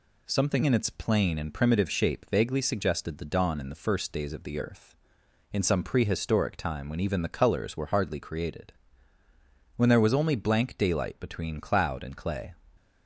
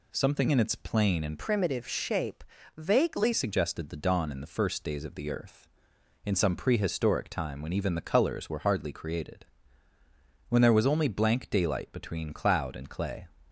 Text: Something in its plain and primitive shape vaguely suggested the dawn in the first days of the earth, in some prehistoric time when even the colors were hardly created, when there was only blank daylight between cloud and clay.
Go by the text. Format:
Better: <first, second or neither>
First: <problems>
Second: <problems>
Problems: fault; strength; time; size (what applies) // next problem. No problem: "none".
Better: first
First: none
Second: changes voice from "primitive" to "vaguely"; from 1.3 to 3.3 s; 2.0 s long // pauses between "shape" and "vaguely"; slight; at 2.4 s; 0.36 s long